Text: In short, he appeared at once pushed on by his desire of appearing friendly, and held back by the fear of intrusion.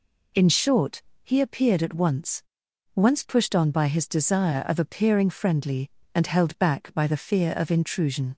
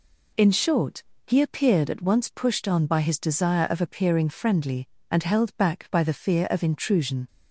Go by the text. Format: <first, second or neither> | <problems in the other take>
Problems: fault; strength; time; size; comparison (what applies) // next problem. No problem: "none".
second | says "once" twice; at 2.9 s